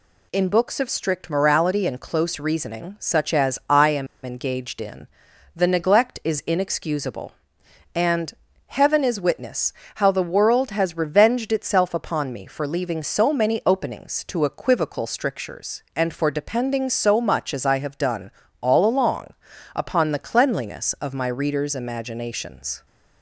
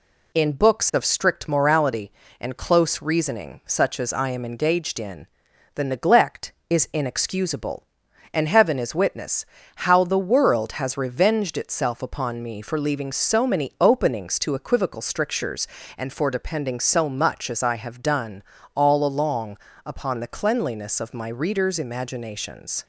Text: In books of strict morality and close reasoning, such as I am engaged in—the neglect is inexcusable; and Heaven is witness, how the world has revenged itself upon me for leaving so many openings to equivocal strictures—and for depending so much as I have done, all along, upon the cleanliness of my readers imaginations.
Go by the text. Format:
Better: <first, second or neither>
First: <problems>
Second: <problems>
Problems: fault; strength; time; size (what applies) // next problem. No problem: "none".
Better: second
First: pauses between "am" and "engaged"; slight; at 4.0 s; 0.16 s long // pauses between "and" and "Heaven"; slight; at 8.3 s; 0.34 s long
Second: none